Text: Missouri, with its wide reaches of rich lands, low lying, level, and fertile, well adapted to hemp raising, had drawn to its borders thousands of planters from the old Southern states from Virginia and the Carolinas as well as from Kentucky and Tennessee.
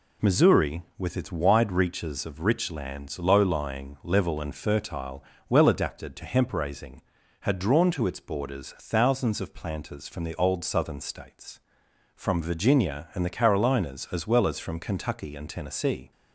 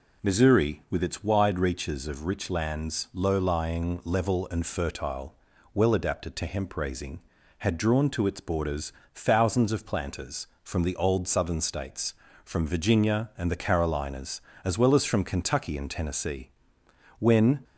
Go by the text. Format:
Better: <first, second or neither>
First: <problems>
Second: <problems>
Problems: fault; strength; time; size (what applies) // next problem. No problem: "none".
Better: first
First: none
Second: pauses between "borders" and "thousands"; slight; at 8.9 s; 0.24 s long // goes on to say "When"; slight; from 17.1 s on; 0.44 s long